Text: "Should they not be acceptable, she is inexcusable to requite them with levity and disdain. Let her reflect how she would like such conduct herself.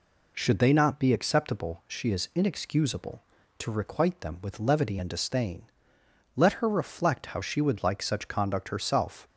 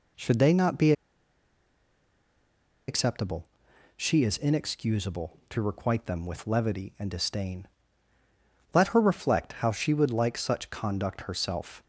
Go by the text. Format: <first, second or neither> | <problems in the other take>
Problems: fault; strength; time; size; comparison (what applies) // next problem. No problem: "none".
first | pauses between "be" and "acceptable"; strong; at 0.9 s; 1.9 s long